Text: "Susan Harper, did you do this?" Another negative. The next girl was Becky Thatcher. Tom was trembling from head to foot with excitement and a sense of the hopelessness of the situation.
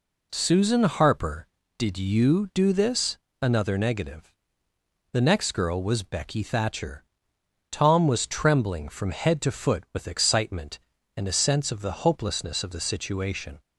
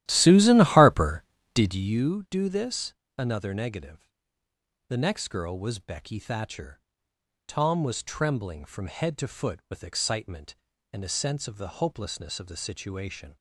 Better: first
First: none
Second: starts louder than the rest; strong; until 2.0 s; 13.5 dB

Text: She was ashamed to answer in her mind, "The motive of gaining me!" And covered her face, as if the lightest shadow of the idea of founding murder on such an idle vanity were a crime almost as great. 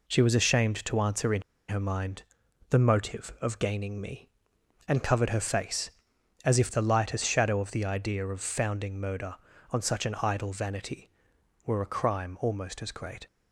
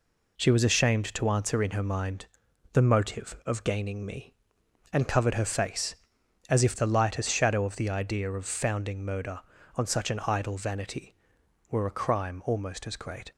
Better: second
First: pauses between "in" and "her"; slight; at 1.4 s; 0.26 s long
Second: none

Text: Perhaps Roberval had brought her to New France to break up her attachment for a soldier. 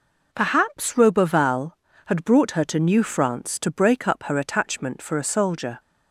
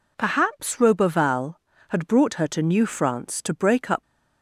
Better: first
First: none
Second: stops before "her attachment for a soldier"; at 4.0 s

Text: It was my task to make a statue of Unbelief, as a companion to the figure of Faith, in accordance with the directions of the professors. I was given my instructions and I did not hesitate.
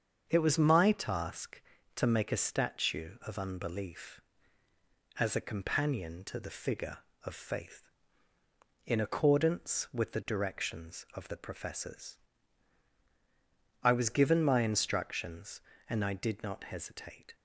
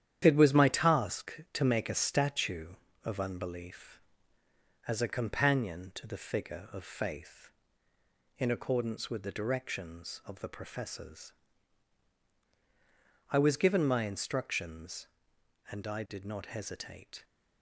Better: first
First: starts louder than the rest; until 1.2 s; 7 dB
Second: gets quieter; throughout; 7 dB // starts louder than the rest; strong; until 1.2 s; 10 dB

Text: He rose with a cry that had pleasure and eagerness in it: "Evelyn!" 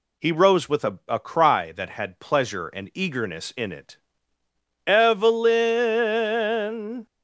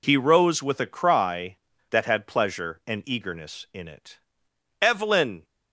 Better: second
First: says "a" twice; at 1.0 s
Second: none

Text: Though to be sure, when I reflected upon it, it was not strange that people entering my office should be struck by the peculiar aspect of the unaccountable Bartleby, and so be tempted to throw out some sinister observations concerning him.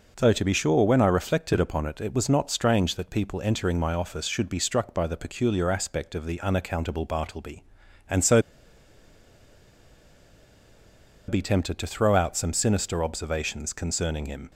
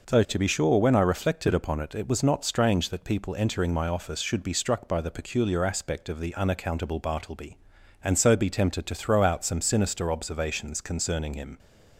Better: second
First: pauses between "so" and "be"; strong; at 8.4 s; 2.8 s long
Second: none

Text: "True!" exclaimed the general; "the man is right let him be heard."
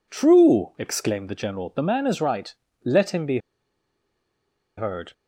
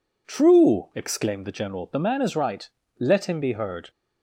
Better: second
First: pauses between "right" and "let"; slight; at 2.5 s; 0.28 s long // pauses between "be" and "heard"; strong; at 3.3 s; 1.3 s long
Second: pauses between "right" and "let"; slight; at 2.6 s; 0.28 s long

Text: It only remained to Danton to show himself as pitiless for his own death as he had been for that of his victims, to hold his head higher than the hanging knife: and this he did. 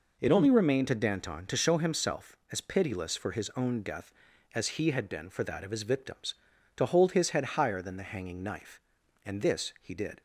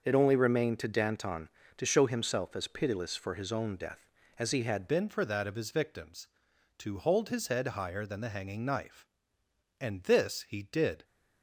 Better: first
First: none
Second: starts louder than the rest; noticeable; until 1.0 s; 6 dB // changes voice at "been"; from 4.8 s on; 6.2 s long

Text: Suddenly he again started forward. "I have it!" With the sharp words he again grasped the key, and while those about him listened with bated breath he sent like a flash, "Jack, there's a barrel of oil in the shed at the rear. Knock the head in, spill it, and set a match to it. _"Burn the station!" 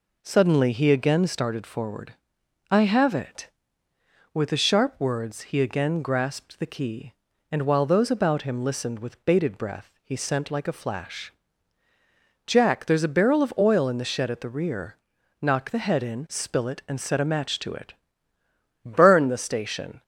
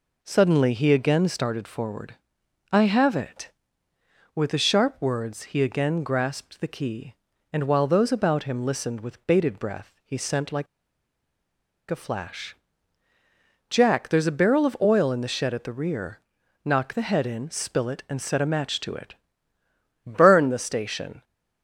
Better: first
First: none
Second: pauses between "like" and "a"; strong; at 10.6 s; 1.2 s long

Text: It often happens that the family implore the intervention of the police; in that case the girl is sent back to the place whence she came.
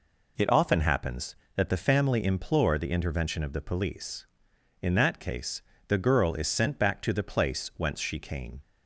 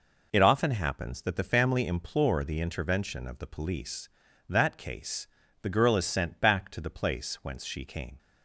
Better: first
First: pauses between "case" and "the"; slight; at 5.6 s; 0.26 s long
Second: skips "in"; at 4.2 s // pauses between "case" and "the"; slight; at 5.2 s; 0.36 s long

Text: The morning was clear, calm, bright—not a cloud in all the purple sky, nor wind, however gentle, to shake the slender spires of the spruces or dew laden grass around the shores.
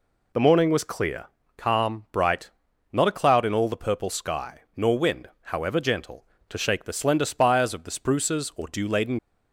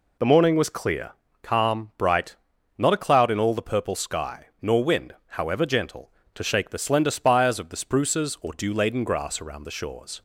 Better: second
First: stops before "grass around the shores"; at 9.1 s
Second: none

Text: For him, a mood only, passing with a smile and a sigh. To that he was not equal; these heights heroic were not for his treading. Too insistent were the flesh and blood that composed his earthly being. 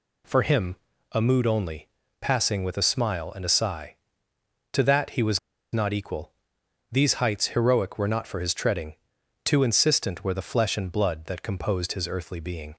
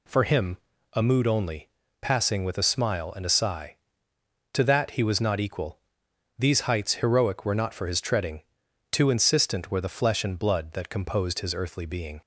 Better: second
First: pauses between "was" and "not"; slight; at 5.3 s; 0.34 s long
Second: none

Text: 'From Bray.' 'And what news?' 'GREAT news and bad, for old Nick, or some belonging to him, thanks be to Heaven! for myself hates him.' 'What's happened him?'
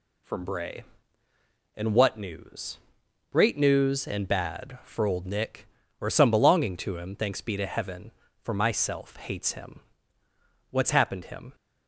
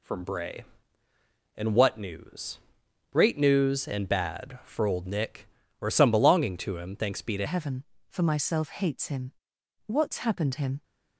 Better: first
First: none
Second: changes voice at "Heaven"; from 7.4 s on; 3.4 s long

